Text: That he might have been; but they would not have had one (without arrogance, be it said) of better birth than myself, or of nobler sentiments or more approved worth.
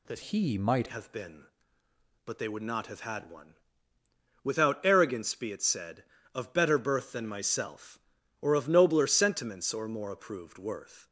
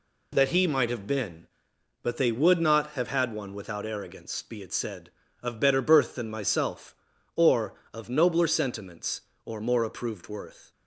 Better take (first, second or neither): second